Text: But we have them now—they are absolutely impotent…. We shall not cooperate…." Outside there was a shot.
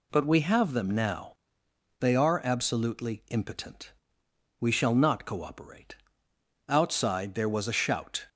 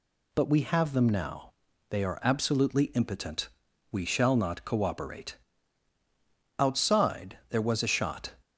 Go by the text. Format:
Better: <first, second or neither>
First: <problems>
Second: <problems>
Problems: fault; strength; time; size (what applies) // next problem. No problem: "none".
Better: second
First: says "shout" for "shot"; at 7.7 s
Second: none